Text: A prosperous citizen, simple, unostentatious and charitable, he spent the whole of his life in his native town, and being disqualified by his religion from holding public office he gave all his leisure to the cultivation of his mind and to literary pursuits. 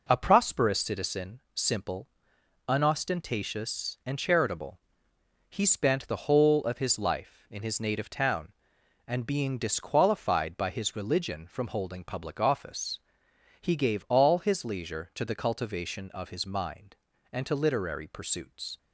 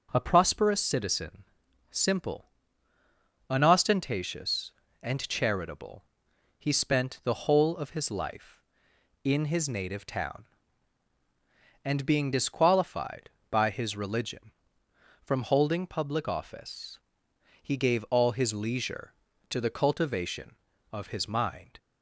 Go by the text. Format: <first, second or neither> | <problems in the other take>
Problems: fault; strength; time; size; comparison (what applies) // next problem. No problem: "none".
first | starts louder than the rest; noticeable; until 1.1 s; 6 dB // pauses between "office" and "he"; noticeable; at 16.9 s; 0.64 s long; noticeable in the first // stops before "and to literary pursuits"; at 21.7 s